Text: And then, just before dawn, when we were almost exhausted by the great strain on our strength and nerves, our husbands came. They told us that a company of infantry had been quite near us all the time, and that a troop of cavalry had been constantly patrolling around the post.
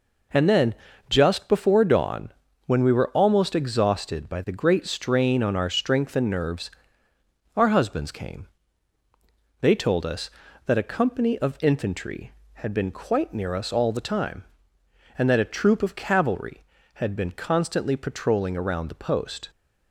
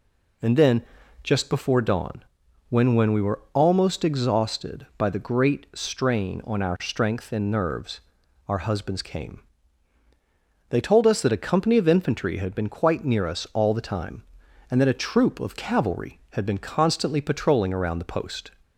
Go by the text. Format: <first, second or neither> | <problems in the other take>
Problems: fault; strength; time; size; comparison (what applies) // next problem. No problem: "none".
first | says "when" twice; at 2.9 s